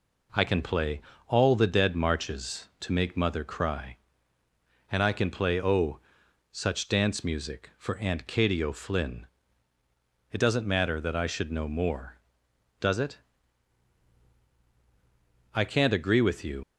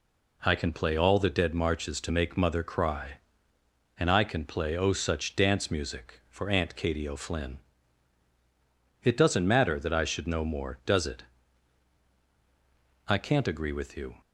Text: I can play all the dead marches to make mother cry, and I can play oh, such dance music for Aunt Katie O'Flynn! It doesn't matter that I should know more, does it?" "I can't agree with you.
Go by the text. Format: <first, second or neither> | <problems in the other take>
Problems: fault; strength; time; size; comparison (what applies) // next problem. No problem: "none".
second | pauses between "play" and "all"; slight; at 1.0 s; 0.26 s long // leaves "you" unfinished; at 16.6 s; 85 ms